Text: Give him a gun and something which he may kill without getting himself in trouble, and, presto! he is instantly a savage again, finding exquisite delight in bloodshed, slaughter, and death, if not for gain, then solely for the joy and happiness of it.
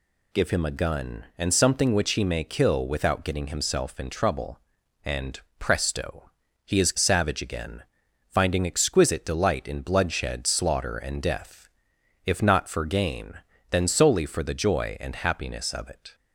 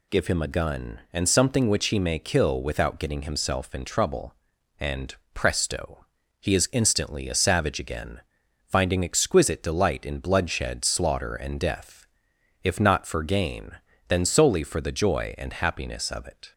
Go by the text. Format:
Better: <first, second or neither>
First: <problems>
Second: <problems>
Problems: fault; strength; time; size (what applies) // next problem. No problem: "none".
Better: second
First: skips "instantly a"; at 6.9 s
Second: none